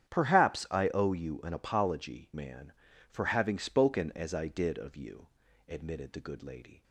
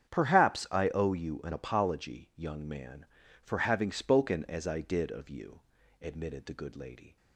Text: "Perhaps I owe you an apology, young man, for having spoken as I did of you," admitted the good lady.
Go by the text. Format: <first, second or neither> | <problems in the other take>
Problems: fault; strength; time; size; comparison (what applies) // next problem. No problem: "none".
second | starts louder than the rest; strong; until 1.2 s; 9.5 dB; strong in the second // skips "young"; at 2.3 s